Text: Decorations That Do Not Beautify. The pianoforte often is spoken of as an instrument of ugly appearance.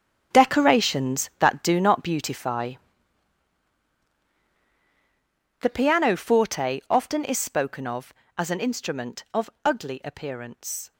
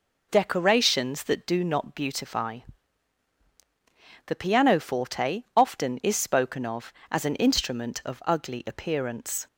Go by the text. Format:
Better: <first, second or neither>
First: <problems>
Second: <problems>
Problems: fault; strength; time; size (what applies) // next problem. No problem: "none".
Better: second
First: gets quieter; strong; throughout; 13.5 dB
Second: none